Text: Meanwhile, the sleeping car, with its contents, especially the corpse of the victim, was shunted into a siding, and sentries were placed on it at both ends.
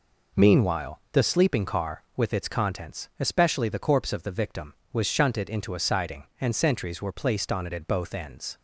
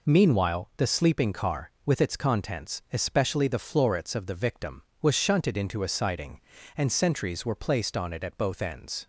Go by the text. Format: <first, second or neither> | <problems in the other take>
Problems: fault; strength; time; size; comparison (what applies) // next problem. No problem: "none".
first | says "florets" for "corpse"; at 3.5 s